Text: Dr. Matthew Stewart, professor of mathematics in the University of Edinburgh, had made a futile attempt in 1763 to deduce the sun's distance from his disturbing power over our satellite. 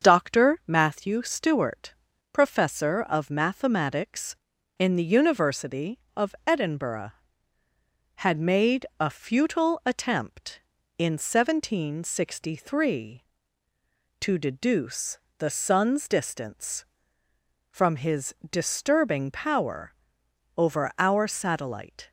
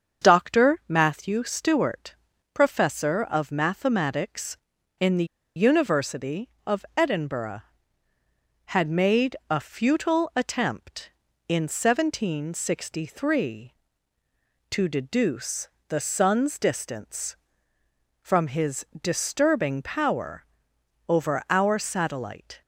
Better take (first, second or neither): first